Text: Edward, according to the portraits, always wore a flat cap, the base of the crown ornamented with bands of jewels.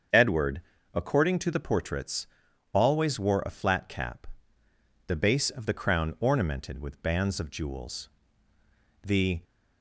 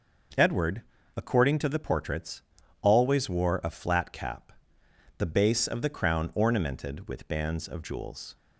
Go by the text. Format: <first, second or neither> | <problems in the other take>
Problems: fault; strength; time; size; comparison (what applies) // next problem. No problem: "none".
second | starts louder than the rest; until 1.4 s; 7 dB // goes on to say "The"; slight; from 9.0 s on; 0.38 s long